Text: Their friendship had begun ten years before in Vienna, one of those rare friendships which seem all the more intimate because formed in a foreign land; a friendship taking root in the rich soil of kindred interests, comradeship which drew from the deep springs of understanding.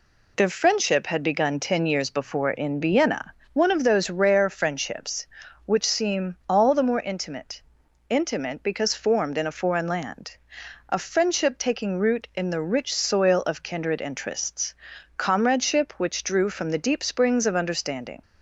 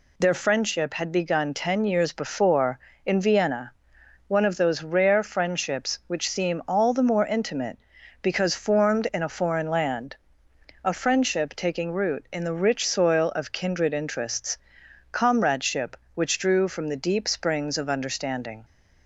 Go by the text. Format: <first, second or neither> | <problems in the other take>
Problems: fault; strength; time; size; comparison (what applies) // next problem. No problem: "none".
second | says "intimate" twice; at 8.0 s